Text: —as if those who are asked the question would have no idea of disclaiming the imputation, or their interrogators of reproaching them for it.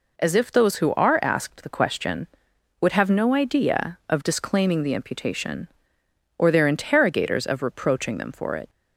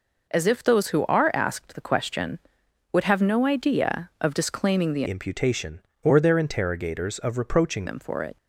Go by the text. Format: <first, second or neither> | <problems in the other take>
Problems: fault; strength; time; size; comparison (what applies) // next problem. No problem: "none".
first | changes voice from "imputation" to "reproaching"; from 5.0 to 7.8 s; 2.8 s long